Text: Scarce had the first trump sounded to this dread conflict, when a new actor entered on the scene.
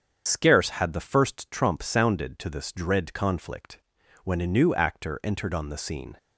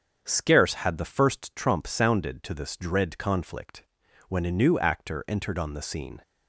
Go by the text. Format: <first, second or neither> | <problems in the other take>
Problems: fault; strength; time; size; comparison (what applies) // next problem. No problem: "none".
second | loses the start of "Scarce"; at 0.2 s; 65 ms // starts louder than the rest; strong; until 1.2 s; 7.5 dB; also in the second